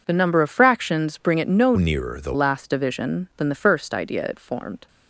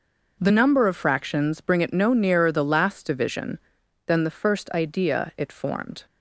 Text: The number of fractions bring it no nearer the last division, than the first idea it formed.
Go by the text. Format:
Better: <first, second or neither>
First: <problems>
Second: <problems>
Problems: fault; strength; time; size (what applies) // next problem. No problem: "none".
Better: second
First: changes voice from "nearer" to "the"; from 1.7 to 2.3 s; 0.6 s long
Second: none